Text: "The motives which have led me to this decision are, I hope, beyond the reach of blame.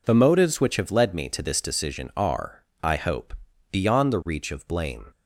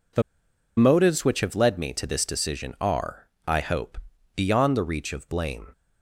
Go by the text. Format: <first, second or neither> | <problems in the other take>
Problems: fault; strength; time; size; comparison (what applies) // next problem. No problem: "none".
first | pauses between "The" and "motives"; noticeable; at 0.2 s; 0.55 s long